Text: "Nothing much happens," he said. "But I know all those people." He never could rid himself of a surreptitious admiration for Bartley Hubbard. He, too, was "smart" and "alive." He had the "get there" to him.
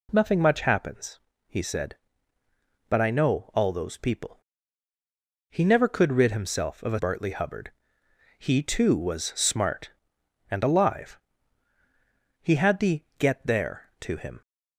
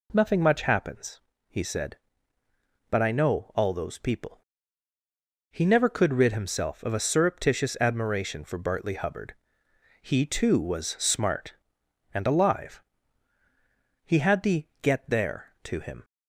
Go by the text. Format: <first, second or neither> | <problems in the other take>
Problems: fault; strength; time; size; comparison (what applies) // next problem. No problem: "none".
second | skips "surreptitious admiration for"; at 6.9 s // pauses between "the" and "get"; slight; at 13.0 s; 0.16 s long; slight in the second